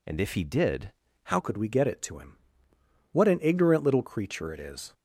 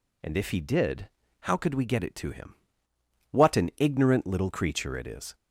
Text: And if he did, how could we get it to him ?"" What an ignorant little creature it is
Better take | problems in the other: second | changes voice at "could"; from 1.3 s on; 3.6 s long

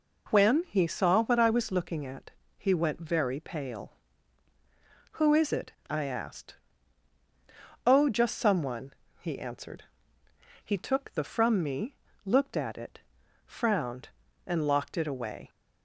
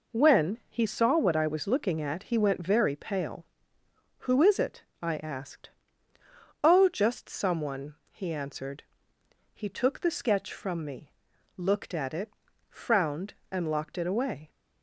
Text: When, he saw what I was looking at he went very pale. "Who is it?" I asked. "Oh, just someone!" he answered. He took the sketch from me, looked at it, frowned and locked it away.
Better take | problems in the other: second | pauses between "at" and "he"; slight; at 2.3 s; 0.26 s long // skips "sketch"; at 11.2 s

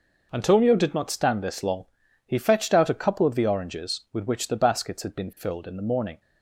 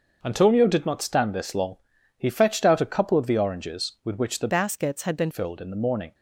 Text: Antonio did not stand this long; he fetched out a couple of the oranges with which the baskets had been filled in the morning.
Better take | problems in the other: first | starts louder than the rest; until 1.2 s; 6 dB // changes voice from "baskets" to "been"; from 4.4 to 5.2 s; 0.8 s long

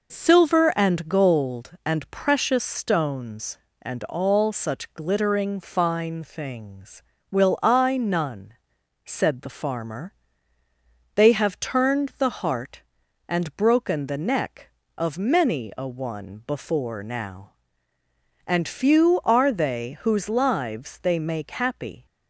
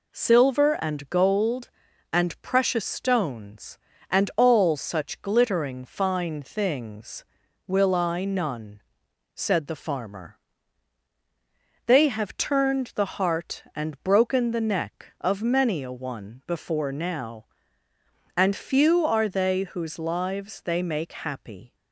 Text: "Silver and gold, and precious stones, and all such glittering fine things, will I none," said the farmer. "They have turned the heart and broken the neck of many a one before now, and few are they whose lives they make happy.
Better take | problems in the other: neither | none

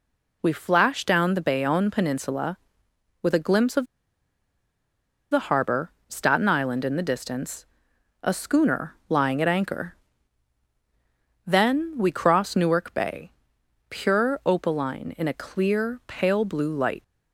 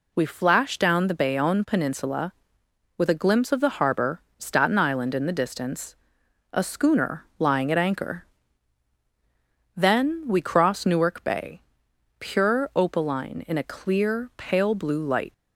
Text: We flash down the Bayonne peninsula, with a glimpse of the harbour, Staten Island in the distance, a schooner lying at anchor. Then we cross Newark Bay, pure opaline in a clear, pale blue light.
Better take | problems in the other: second | pauses between "of" and "the"; strong; at 3.8 s; 1.4 s long

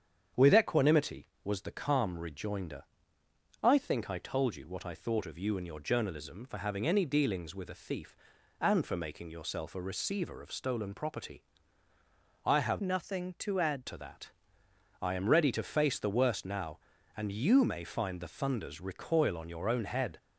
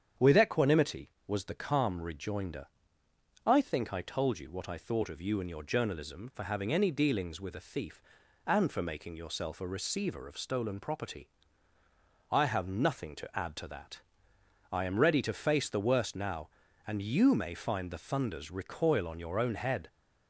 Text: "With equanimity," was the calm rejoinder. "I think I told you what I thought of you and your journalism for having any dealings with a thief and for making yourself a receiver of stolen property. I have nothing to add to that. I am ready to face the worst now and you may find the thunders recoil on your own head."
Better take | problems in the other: second | starts louder than the rest; strong; until 1.5 s; 8 dB; strong in the second // changes voice from "nothing" to "add"; from 12.8 to 13.8 s; 1.0 s long

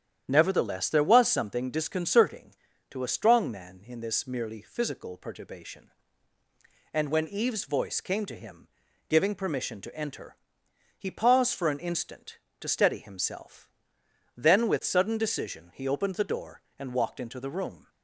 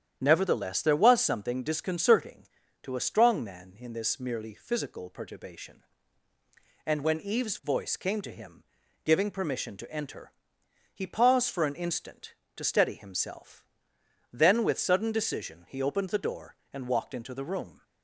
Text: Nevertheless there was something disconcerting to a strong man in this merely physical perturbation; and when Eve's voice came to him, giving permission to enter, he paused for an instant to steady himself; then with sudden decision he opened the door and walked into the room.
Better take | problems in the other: neither | starts louder than the rest; strong; the same in both

